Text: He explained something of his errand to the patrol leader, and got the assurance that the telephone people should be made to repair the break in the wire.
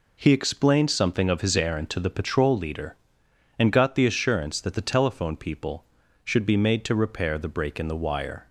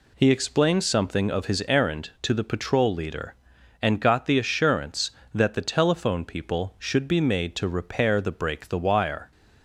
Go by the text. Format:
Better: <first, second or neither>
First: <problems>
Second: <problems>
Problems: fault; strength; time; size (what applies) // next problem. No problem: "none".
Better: first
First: none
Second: skips "in"; at 8.6 s